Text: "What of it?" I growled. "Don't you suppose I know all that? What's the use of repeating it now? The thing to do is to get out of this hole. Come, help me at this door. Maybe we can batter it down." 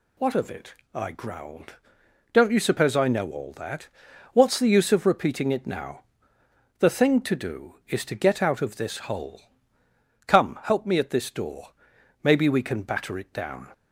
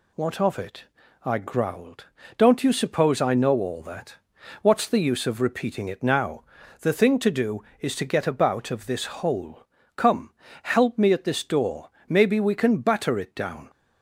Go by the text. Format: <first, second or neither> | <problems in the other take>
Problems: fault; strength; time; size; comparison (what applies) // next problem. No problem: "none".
first | says "about" for "out"; at 8.2 s